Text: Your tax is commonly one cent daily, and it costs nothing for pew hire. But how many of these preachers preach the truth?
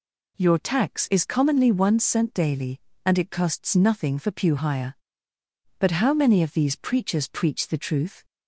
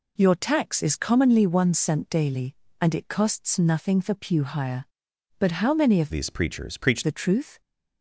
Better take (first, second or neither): first